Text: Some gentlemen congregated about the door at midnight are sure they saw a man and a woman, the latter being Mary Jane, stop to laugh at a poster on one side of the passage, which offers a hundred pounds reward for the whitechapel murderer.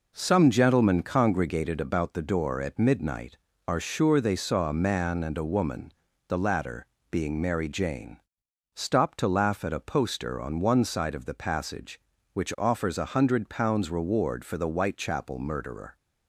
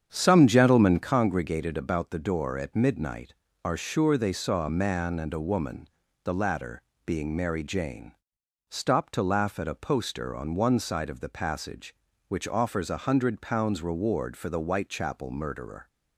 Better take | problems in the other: first | starts louder than the rest; strong; until 1.1 s; 8 dB // pauses between "latter" and "being"; slight; at 6.8 s; 0.23 s long; slight in the first

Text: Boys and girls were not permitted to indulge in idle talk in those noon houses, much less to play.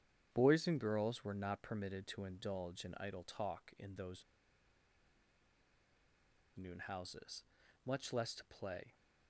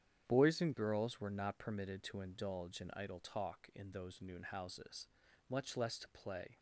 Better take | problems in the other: second | starts louder than the rest; strong; until 1.3 s; 9 dB; strong in the second // pauses between "those" and "noon"; strong; at 4.2 s; 2.3 s long

